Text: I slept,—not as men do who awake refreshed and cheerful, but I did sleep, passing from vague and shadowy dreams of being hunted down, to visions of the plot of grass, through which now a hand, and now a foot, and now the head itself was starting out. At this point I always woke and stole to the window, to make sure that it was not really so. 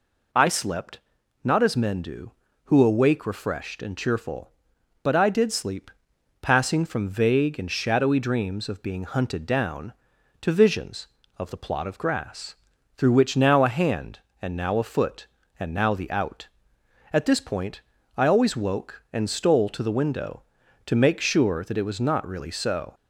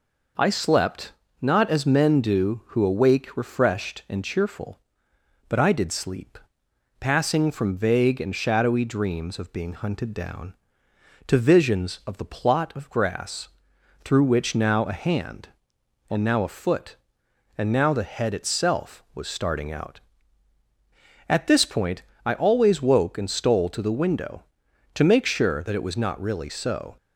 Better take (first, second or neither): second